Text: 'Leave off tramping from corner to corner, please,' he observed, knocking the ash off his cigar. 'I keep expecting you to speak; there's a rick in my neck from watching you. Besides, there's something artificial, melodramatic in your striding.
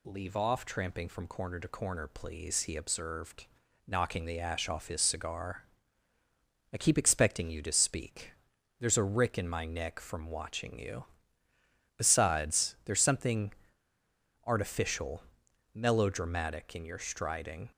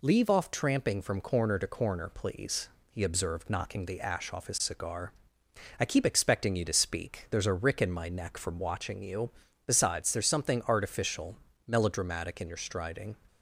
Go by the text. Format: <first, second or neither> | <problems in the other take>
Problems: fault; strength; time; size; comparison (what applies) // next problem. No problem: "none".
second | pauses between "something" and "artificial"; noticeable; at 13.5 s; 0.94 s long